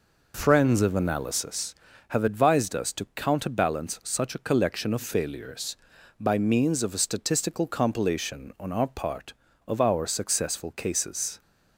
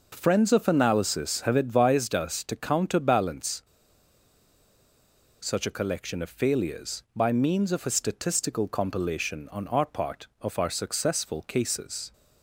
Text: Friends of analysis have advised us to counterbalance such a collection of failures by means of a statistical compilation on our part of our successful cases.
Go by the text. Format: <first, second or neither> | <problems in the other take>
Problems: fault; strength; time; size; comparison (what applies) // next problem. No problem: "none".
first | pauses between "counterbalance" and "such"; strong; at 3.6 s; 1.7 s long